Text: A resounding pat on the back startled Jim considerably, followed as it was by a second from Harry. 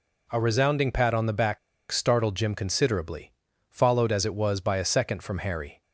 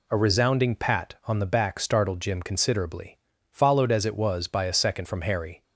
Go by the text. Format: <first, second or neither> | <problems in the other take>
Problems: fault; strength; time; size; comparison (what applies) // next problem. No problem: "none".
second | pauses between "back" and "startled"; slight; at 1.5 s; 0.33 s long